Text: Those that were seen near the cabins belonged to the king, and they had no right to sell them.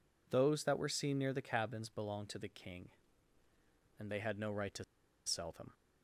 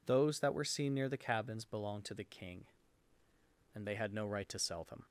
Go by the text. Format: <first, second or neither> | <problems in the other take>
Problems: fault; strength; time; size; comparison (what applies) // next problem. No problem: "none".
second | pauses between "to" and "sell"; at 4.8 s; 0.42 s long